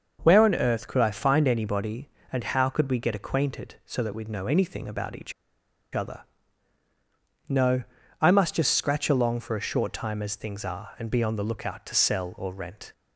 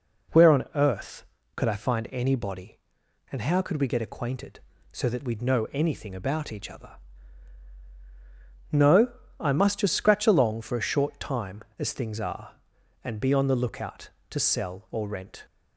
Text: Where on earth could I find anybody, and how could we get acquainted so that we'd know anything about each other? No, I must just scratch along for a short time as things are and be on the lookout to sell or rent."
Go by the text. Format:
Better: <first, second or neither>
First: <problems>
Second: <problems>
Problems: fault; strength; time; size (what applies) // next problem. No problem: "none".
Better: second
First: starts louder than the rest; noticeable; until 1.2 s; 6 dB // pauses between "each" and "other"; noticeable; at 5.3 s; 0.61 s long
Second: none